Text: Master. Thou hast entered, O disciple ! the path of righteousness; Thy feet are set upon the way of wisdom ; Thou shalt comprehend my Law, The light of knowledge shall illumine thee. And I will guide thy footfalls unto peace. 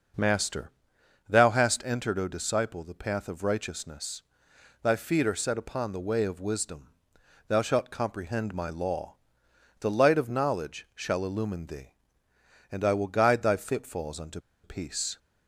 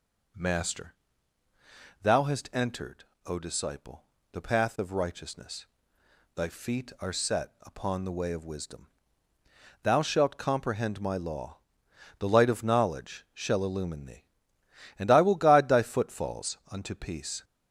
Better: second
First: starts louder than the rest; until 1.7 s; 6 dB // pauses between "unto" and "peace"; slight; at 14.3 s; 0.24 s long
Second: none

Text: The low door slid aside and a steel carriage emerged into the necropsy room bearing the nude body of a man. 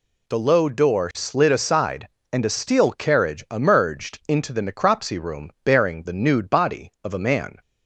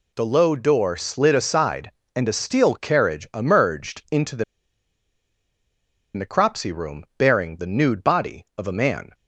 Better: first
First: none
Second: pauses between "the" and "necropsy"; strong; at 4.4 s; 1.7 s long

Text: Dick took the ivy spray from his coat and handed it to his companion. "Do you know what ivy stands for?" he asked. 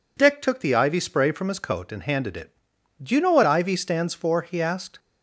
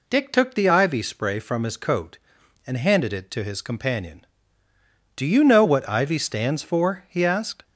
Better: second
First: skips "to his companion"; at 2.7 s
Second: none

